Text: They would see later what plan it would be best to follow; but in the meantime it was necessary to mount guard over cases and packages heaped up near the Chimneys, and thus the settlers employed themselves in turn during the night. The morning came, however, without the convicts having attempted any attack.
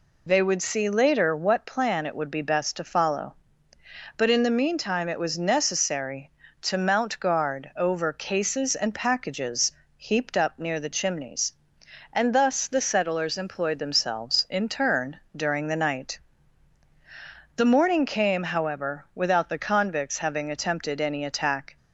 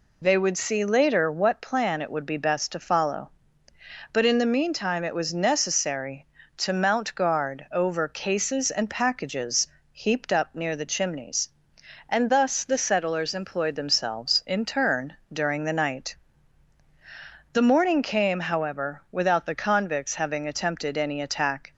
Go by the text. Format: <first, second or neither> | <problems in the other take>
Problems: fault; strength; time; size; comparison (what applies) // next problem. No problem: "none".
neither | pauses between "packages" and "heaped"; slight; the same in both // pauses between "turn" and "during"; slight; the same in both